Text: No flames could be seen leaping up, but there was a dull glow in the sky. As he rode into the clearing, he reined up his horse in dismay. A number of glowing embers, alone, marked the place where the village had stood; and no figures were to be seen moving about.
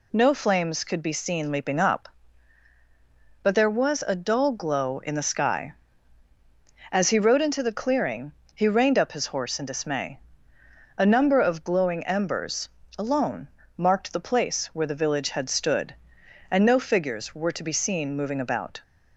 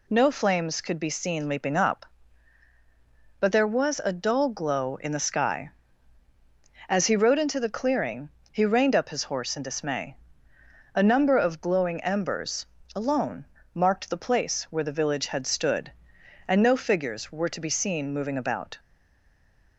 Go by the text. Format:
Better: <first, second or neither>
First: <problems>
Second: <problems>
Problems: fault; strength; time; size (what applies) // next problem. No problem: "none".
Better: first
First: none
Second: stays silent after the last word; from 18.7 s on; 1.0 s long